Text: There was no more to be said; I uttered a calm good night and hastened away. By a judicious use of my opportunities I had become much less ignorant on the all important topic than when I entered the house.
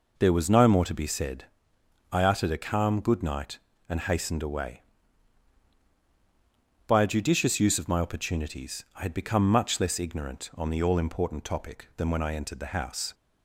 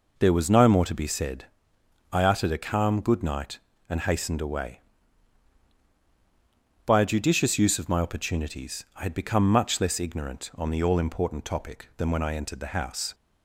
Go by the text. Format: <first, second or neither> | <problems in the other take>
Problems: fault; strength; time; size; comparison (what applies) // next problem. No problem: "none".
neither | none